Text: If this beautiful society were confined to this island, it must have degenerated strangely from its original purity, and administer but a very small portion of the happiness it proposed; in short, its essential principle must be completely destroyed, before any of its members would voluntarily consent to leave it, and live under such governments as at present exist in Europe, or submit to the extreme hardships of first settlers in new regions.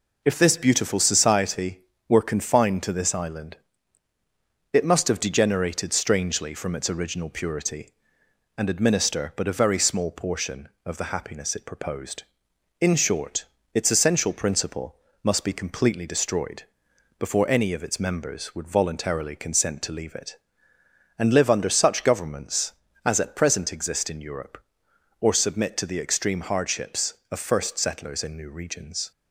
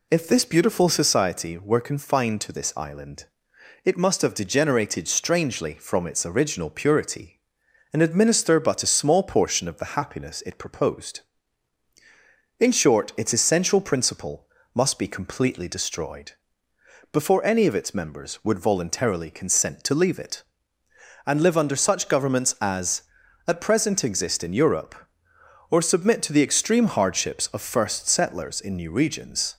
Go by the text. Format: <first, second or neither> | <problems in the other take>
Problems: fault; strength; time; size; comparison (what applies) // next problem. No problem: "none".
first | skips "very"; at 8.9 s // pauses between "principle" and "must"; slight; at 14.4 s; 0.26 s long; slight in the first